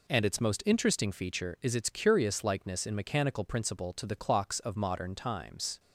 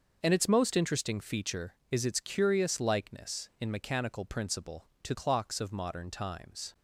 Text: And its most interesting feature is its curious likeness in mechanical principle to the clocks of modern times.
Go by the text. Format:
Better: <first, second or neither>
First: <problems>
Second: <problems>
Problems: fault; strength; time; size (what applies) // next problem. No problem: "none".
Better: first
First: none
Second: starts louder than the rest; until 1.2 s; 6.5 dB // skips "the"; at 5.1 s